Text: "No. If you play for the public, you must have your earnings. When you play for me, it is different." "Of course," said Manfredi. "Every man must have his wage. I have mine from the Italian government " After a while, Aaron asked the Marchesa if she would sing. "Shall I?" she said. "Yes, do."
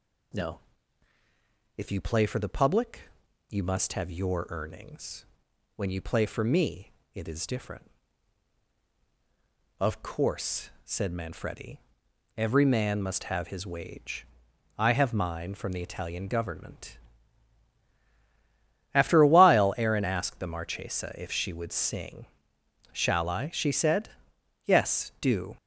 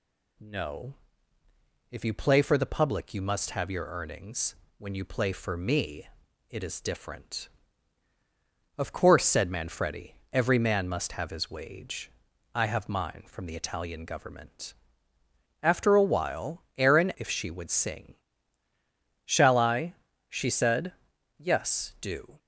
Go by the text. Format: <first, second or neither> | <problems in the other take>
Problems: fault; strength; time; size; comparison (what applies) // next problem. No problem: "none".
first | skips "asked the Marchesa"; at 17.1 s